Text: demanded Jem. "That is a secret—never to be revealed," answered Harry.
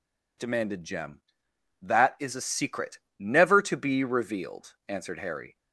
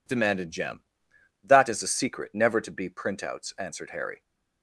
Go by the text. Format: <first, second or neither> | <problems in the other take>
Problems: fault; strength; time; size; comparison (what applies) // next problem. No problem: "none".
first | says "printouts" for "revealed"; at 2.8 s